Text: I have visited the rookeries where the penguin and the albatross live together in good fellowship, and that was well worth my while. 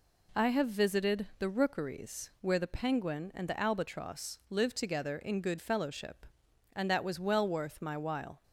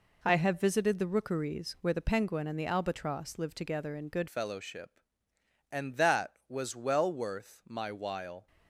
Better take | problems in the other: first | changes voice at "fellowship"; from 4.2 s on; 4.2 s long

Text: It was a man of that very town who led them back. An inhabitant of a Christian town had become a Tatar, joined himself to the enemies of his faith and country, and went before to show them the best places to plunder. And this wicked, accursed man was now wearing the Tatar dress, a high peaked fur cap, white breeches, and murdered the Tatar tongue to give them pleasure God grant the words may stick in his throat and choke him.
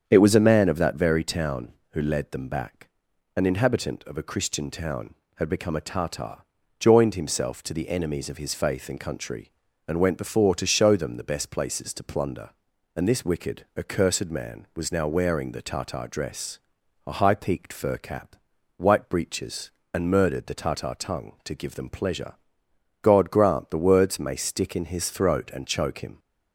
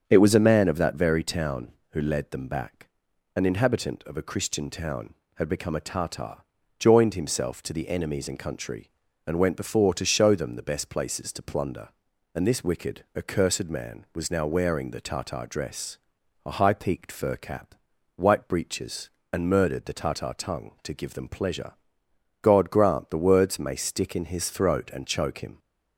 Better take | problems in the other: first | starts louder than the rest; strong; until 1.0 s; 7.5 dB; strong in the first // skips "of his faith"; at 8.2 s // pauses between "pleasure" and "God"; noticeable; at 21.7 s; 0.66 s long; noticeable in the first

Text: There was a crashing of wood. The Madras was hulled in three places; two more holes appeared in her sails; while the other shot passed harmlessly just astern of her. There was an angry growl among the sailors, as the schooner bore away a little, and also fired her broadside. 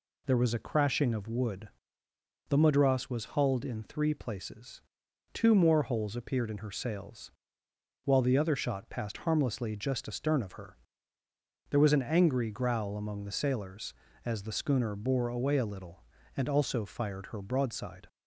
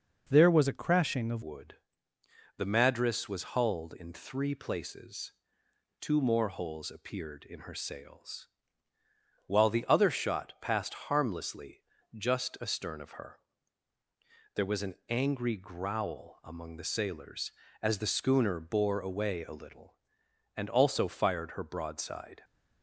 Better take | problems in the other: first | changes voice at "wood"; from 1.4 s on; 21.0 s long // pauses between "harmlessly" and "just"; slight; at 11.8 s; 0.30 s long

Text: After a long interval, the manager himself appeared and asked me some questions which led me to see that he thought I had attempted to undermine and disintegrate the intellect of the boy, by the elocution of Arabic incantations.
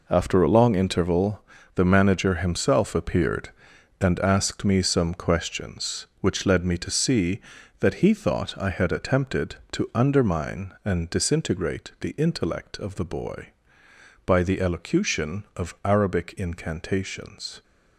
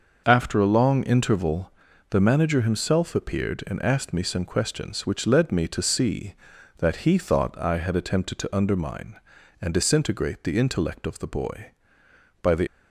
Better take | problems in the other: first | starts louder than the rest; noticeable; until 1.2 s; 6 dB // stops before "elocution of Arabic incantations"; at 12.6 s

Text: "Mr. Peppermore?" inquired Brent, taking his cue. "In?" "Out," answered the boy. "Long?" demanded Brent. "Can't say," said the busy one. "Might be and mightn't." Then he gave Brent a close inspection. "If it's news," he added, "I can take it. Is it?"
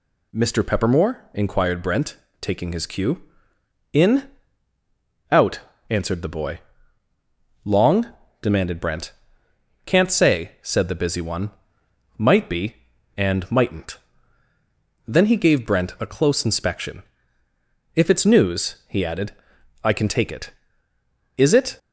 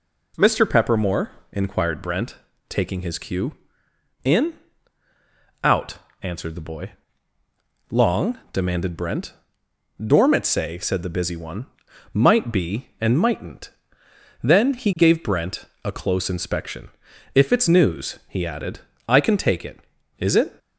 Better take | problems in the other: first | says "Dormit" for "Can't"; at 9.9 s // pauses between "Brent" and "a"; slight; at 15.6 s; 0.20 s long

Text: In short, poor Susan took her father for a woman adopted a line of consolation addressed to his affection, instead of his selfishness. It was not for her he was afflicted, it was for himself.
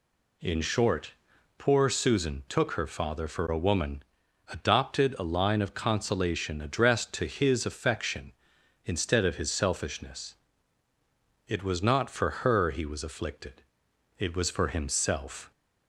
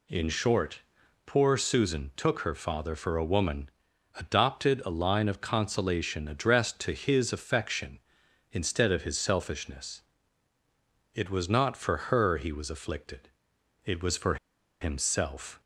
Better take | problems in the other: first | pauses between "woman" and "adopted"; noticeable; at 3.6 s; 0.46 s long; noticeable in the first // pauses between "for" and "himself"; at 14.3 s; 0.45 s long

